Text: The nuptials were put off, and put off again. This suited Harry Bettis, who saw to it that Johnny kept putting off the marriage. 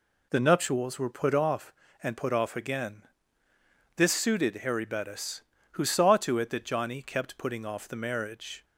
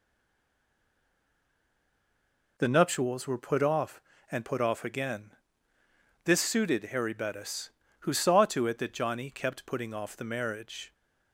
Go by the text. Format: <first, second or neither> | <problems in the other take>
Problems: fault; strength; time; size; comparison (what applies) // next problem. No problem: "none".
first | stays silent before the first word; strong; until 2.5 s; 2.5 s long